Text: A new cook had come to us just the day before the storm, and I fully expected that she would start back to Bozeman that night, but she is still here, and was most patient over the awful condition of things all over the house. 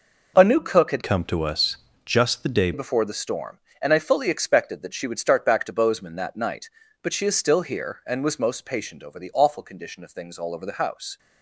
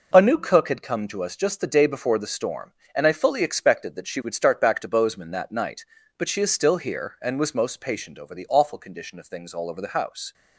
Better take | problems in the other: second | changes voice from "come" to "day"; from 1.0 to 2.7 s; 1.7 s long // pauses between "us" and "just"; slight; at 1.7 s; 0.30 s long

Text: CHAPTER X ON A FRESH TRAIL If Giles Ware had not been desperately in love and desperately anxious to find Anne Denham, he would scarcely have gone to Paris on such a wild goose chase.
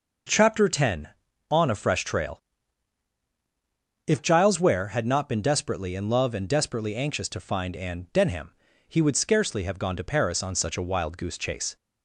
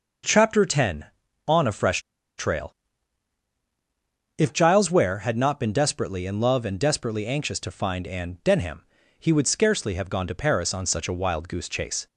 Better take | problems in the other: first | pauses between "FRESH" and "TRAIL"; at 2.0 s; 0.37 s long // pauses between "TRAIL" and "If"; strong; at 2.7 s; 1.6 s long; strong in the first

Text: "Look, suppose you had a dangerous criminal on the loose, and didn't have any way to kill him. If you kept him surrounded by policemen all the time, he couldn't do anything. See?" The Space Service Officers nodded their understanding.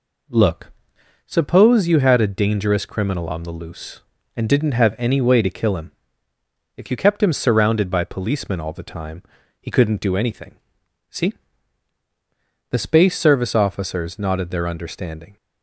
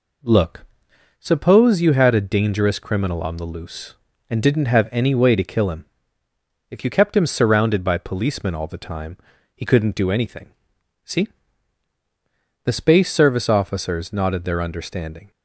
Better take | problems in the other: neither | none

